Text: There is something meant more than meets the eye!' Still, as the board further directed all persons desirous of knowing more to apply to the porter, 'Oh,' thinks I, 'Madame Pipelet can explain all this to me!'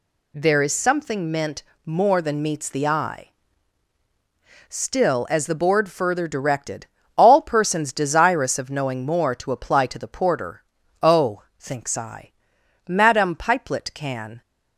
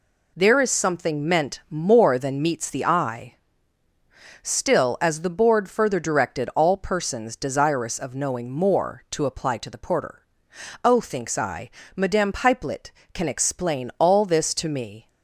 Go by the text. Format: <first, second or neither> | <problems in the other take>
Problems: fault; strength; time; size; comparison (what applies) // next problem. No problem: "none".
second | pauses between "meant" and "more"; slight; at 1.6 s; 0.22 s long // pauses between "directed" and "all"; slight; at 6.8 s; 0.30 s long // stops before "explain all this to me"; at 14.4 s